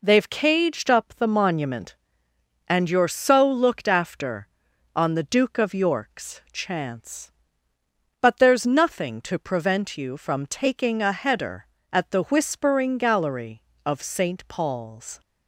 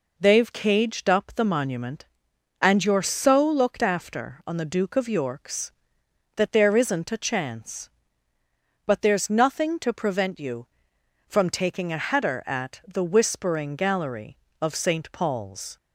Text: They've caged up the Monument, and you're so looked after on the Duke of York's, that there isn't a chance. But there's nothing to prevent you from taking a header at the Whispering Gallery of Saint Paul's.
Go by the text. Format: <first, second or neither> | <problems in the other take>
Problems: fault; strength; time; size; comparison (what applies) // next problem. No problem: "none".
second | skips "that there isn't a"; at 6.4 s